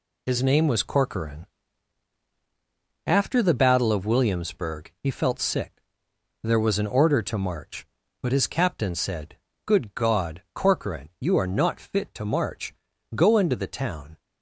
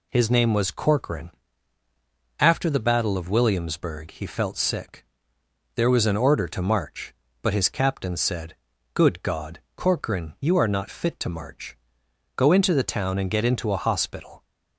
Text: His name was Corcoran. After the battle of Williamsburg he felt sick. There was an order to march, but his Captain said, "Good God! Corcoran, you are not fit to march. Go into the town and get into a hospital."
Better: second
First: stops before "and get into a hospital"; at 14.1 s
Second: none

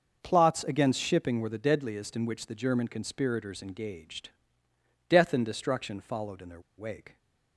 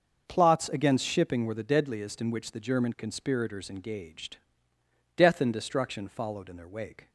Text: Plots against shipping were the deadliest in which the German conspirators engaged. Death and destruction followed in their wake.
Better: second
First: pauses between "their" and "wake"; slight; at 6.5 s; 0.18 s long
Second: none

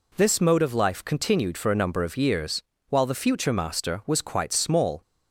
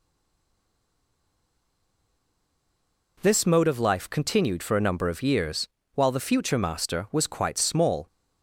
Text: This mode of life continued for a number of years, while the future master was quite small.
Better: first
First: none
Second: stays silent before the first word; strong; until 3.1 s; 3.1 s long

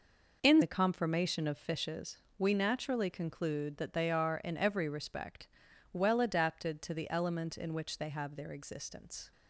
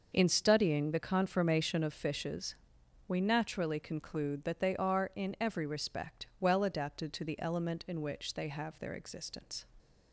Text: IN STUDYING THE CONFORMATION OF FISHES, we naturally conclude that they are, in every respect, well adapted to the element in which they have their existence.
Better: second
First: skips "STUDYING"; at 0.6 s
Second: none

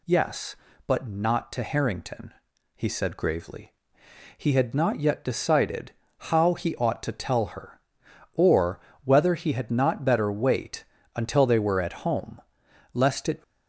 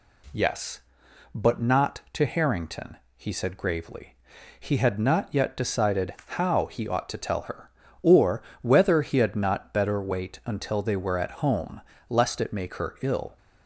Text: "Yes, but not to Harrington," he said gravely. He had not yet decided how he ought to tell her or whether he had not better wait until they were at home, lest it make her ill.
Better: second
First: pauses between "decided" and "how"; slight; at 5.9 s; 0.24 s long // pauses between "or" and "whether"; slight; at 8.8 s; 0.24 s long // pauses between "wait" and "until"; slight; at 10.8 s; 0.32 s long // stops before "make her ill"; at 13.4 s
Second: pauses between "or" and "whether"; slight; at 8.4 s; 0.20 s long

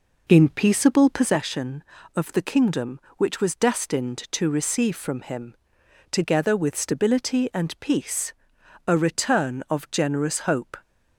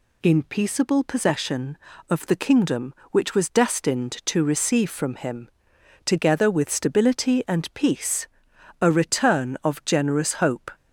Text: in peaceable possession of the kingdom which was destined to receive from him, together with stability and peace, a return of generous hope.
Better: second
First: starts louder than the rest; noticeable; until 1.3 s; 4.5 dB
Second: none

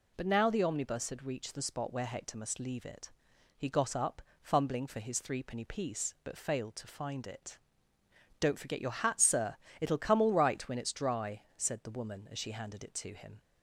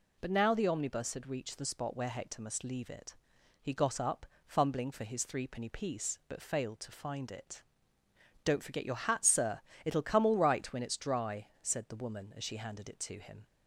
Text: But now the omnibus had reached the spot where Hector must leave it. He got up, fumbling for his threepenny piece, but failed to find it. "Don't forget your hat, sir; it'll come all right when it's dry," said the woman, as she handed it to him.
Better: neither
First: none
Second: none

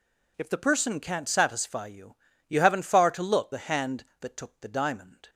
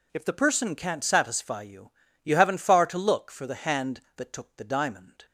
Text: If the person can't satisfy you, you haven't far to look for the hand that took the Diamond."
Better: second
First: skips "for"; at 3.5 s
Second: none

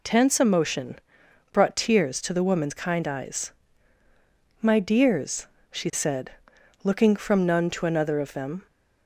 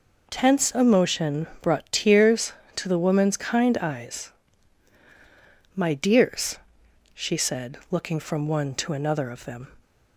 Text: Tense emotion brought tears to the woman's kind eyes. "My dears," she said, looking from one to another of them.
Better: second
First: pauses between "emotion" and "brought"; noticeable; at 0.9 s; 0.52 s long // says "none" for "one"; at 7.4 s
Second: pauses between "emotion" and "brought"; slight; at 1.4 s; 0.16 s long

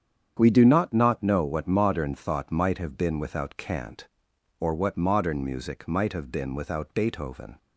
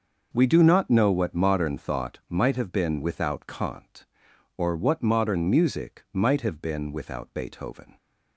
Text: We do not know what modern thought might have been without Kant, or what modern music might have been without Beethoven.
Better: second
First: starts louder than the rest; strong; until 1.3 s; 8 dB // says "not" twice; at 0.9 s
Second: none

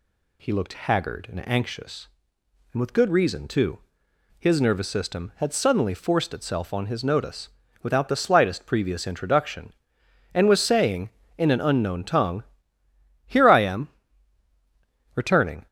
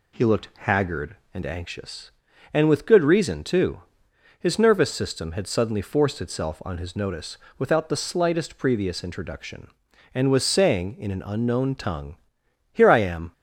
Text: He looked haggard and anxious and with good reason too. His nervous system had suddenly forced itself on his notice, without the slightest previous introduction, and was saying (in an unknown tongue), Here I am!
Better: second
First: goes on to say "Returning"; from 15.1 s on; 0.52 s long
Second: none

